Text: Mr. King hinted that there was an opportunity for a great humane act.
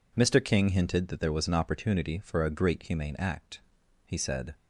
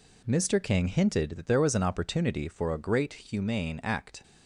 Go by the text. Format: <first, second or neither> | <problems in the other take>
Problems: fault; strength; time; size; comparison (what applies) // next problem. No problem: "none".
second | goes on to say "He said"; from 4.0 s on; 0.50 s long